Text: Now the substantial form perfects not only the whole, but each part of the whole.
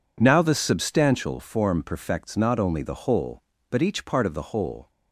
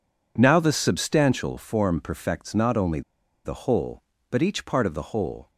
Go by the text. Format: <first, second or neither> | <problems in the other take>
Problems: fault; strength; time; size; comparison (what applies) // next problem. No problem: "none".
first | pauses between "only" and "the"; at 3.0 s; 0.44 s long